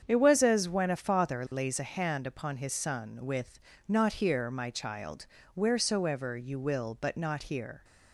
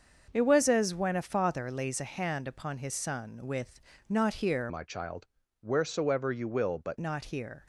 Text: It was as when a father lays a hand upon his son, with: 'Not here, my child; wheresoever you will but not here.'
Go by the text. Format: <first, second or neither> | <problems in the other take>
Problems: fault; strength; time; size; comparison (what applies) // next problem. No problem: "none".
first | starts louder than the rest; until 1.3 s; 6.5 dB; strong in the first // changes voice from "my" to "but"; from 4.6 to 6.9 s; 2.3 s long